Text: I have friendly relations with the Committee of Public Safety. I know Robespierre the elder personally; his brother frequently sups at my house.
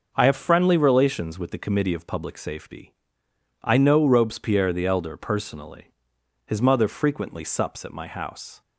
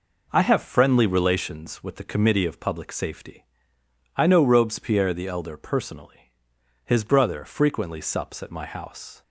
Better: second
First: says "mother" for "brother"; at 6.6 s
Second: none

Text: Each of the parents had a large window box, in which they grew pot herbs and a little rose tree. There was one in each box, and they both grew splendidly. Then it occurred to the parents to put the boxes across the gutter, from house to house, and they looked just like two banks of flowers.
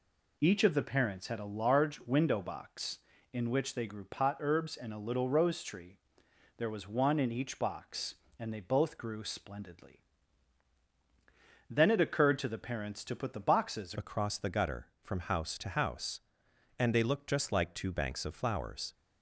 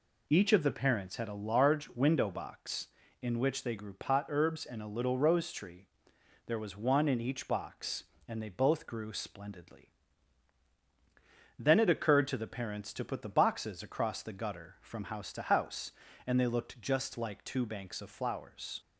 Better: second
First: changes voice at "across"; from 13.9 s on; 5.0 s long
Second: none

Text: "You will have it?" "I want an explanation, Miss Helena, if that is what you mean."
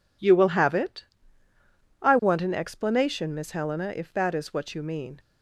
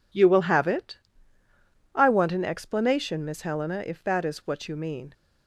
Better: neither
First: none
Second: none

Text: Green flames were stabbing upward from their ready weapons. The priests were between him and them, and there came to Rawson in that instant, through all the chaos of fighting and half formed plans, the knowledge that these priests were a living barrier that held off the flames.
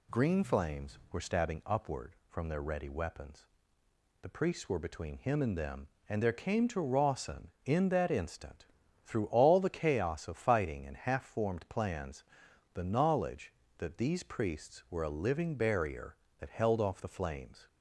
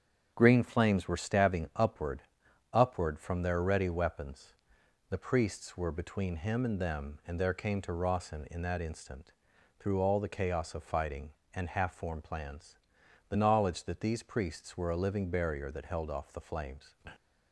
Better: first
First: none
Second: starts louder than the rest; strong; until 1.3 s; 8 dB // says "upward" twice; at 2.7 s

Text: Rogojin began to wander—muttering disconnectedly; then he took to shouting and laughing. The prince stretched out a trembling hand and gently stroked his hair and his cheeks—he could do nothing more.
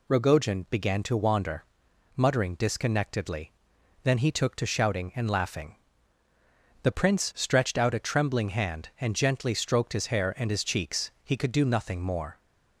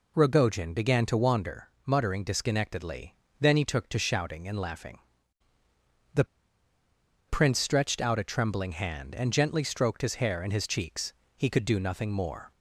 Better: first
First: none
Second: pauses between "The" and "prince"; at 6.2 s; 1.0 s long

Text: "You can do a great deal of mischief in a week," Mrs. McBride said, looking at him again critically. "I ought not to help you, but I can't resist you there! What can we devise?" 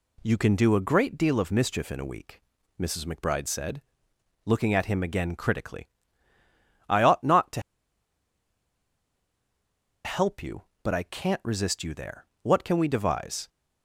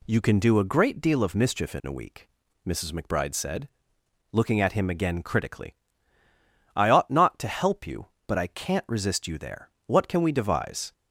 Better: second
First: pauses between "to" and "help"; strong; at 7.6 s; 2.4 s long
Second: none

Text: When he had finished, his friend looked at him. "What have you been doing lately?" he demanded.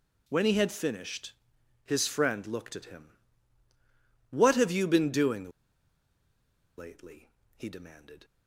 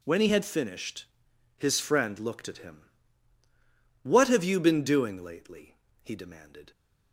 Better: second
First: pauses between "doing" and "lately"; strong; at 5.4 s; 1.2 s long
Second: none

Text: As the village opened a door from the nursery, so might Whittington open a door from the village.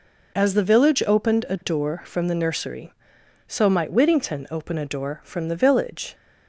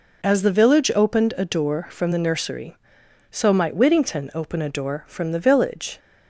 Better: neither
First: none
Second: none

